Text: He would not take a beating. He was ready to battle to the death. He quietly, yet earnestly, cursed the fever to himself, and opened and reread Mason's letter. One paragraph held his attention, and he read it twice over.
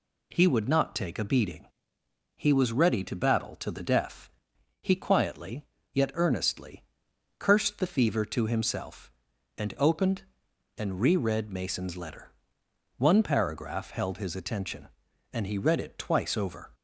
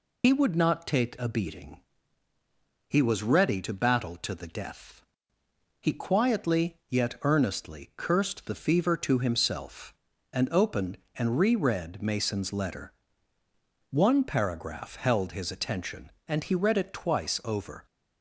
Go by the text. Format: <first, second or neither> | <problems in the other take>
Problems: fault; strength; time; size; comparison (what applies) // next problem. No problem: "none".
first | loses the start of "He"; at 0.2 s; 80 ms